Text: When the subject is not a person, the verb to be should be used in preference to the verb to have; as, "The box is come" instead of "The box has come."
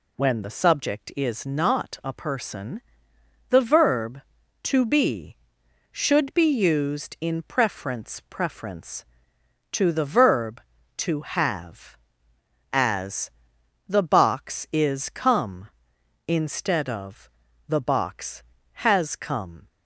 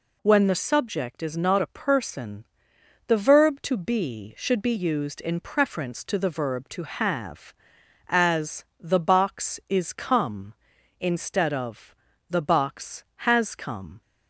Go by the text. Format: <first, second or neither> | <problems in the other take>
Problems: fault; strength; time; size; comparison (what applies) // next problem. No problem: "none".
second | says "preference" twice; at 8.2 s // pauses between "of" and "The"; at 17.2 s; 0.38 s long; also in the second